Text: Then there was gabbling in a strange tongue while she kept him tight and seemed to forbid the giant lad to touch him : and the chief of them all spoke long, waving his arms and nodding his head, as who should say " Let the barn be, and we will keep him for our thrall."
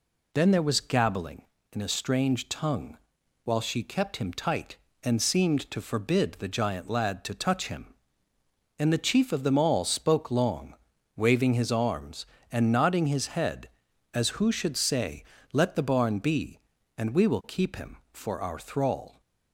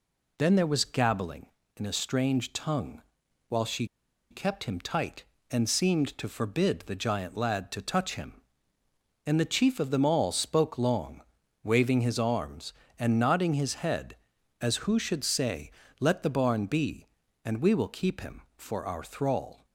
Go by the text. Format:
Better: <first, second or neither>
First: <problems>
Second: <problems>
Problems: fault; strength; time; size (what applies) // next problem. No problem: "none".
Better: first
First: pauses between "tongue" and "while"; noticeable; at 2.9 s; 0.46 s long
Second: pauses between "tongue" and "while"; noticeable; at 3.0 s; 0.46 s long // pauses between "she" and "kept"; at 3.8 s; 0.44 s long